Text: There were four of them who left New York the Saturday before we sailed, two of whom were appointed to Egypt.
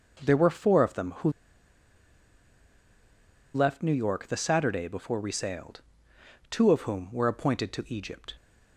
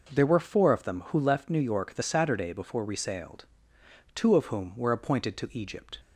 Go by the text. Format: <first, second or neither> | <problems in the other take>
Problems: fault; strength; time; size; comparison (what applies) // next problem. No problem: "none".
second | pauses between "who" and "left"; strong; at 1.2 s; 2.2 s long